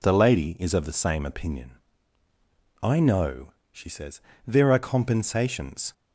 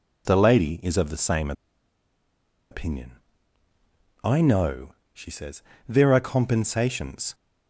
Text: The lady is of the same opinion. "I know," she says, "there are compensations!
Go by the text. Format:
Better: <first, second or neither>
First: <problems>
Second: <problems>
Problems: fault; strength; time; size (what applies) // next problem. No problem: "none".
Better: first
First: none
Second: pauses between "same" and "opinion"; at 1.5 s; 1.1 s long